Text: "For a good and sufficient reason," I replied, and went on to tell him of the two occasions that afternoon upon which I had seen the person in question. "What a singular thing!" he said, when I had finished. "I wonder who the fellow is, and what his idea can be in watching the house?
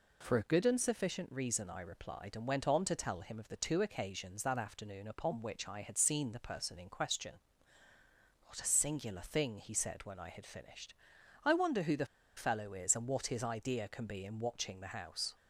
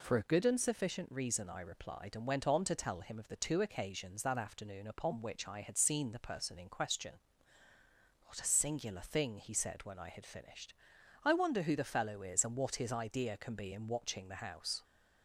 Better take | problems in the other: second | pauses between "the" and "fellow"; slight; at 12.0 s; 0.31 s long

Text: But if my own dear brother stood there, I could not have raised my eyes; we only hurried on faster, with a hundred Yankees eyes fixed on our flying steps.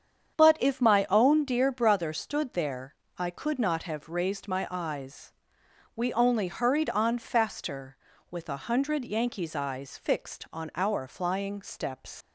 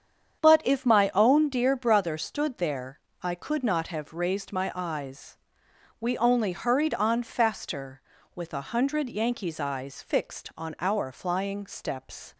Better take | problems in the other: second | starts louder than the rest; strong; until 1.4 s; 8 dB; strong in the second // leaves "steps" unfinished; at 12.2 s; 100 ms

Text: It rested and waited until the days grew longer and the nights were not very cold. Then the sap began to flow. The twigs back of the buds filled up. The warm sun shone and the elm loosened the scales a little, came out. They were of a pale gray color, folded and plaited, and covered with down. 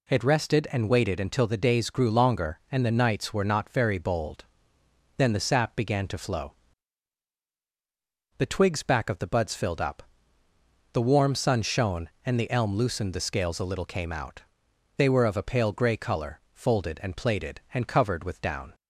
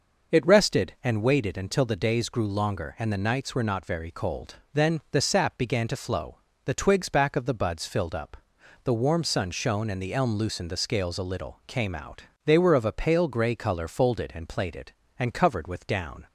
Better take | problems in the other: second | says "bold" for "cold"; at 3.9 s

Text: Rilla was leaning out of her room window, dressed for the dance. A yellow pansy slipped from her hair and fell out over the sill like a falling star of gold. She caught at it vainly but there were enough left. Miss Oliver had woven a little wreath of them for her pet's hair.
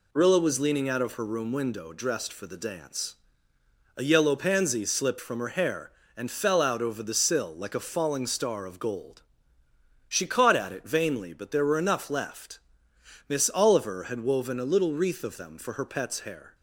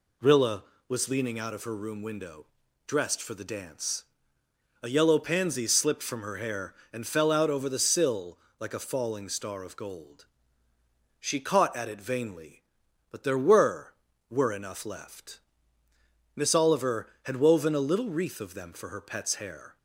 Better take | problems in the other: first | pauses between "sill" and "like"; slight; at 8.3 s; 0.22 s long // says "were" twice; at 14.2 s

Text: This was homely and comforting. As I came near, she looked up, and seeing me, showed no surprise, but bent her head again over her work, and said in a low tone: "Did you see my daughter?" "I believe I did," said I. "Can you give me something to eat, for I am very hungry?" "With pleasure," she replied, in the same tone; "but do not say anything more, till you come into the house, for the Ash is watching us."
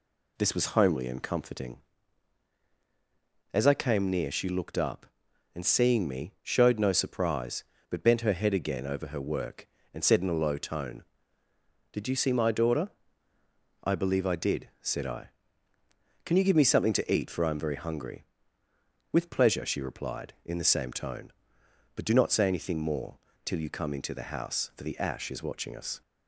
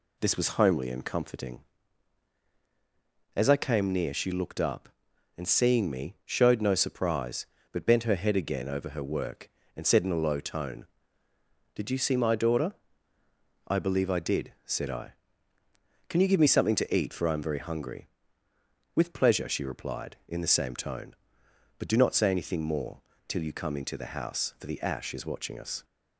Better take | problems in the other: neither | none

